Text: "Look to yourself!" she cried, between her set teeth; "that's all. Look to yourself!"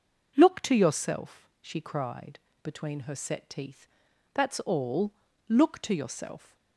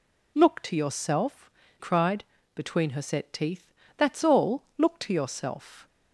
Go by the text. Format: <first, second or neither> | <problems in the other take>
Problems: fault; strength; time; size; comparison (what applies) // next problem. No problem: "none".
first | skips "she"; at 1.6 s